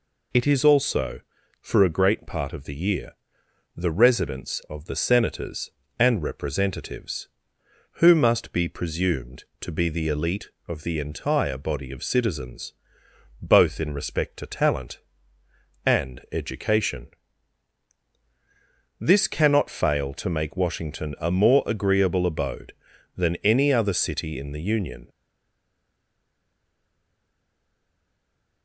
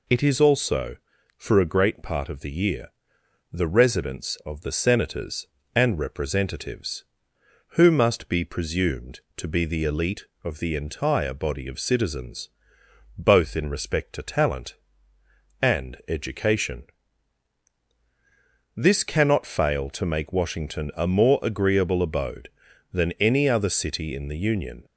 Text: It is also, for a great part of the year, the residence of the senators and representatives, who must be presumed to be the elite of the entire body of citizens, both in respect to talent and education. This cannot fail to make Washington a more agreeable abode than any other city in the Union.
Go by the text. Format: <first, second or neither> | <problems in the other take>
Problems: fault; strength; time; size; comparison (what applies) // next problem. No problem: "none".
second | stays silent after the last word; strong; from 25.0 s on; 3.6 s long